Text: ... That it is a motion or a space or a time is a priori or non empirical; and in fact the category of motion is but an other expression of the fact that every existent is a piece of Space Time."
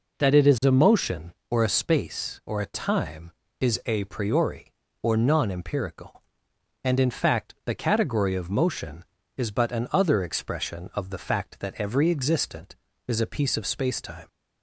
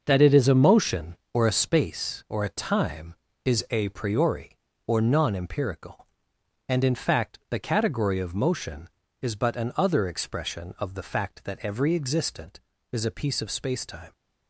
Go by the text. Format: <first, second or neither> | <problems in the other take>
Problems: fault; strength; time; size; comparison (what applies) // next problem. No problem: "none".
first | gets quieter; strong; throughout; 8 dB